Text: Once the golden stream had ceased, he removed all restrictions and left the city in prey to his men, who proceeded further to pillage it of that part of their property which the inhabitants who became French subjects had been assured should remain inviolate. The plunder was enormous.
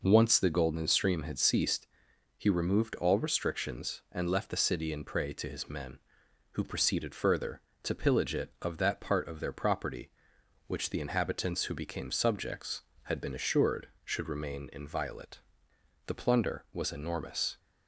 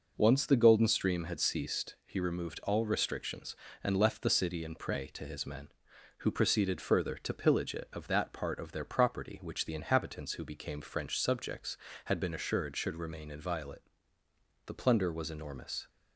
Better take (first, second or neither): second